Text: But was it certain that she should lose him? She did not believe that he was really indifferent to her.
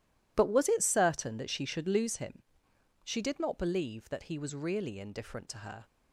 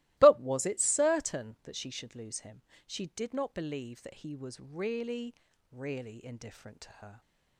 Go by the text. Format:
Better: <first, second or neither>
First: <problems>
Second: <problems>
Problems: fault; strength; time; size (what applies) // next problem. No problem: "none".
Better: first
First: none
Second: starts louder than the rest; strong; until 1.1 s; 18 dB // says "really" twice; at 5.7 s